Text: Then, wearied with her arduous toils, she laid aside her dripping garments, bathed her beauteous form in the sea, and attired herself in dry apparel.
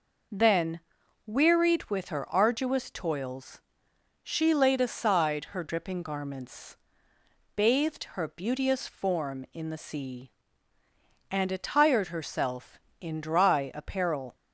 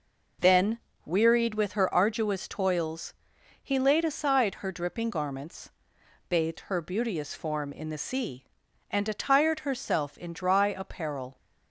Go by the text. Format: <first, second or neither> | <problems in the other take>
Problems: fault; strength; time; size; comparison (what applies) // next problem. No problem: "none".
first | says "he" for "she"; at 3.6 s